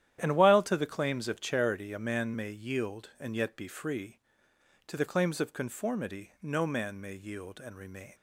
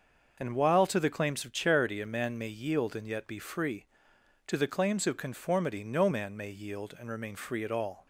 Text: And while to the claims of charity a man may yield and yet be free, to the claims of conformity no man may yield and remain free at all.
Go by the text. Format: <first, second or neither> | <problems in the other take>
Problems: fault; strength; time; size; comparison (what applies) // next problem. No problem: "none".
second | starts louder than the rest; strong; until 1.2 s; 11 dB; also in the second // stops before "free at all"; at 8.1 s